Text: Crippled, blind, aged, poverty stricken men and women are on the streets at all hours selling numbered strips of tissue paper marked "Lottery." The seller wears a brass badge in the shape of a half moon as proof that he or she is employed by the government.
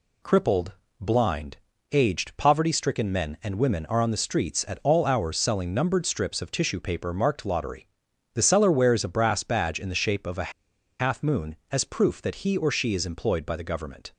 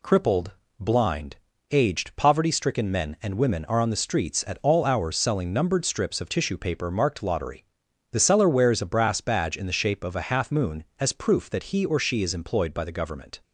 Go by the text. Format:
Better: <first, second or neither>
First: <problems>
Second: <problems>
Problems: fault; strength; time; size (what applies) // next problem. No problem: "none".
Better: second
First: pauses between "a" and "half"; noticeable; at 10.5 s; 0.49 s long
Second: none